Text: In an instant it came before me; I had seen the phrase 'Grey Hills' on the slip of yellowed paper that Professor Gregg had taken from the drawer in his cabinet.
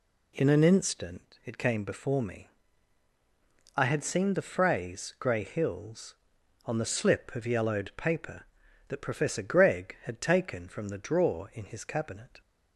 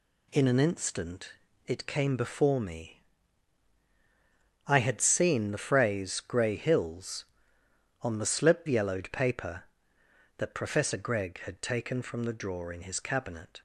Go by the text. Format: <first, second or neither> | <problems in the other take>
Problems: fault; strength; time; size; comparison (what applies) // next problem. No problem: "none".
first | pauses between "instant" and "it"; slight; at 1.3 s; 0.34 s long // skips "of"; at 8.6 s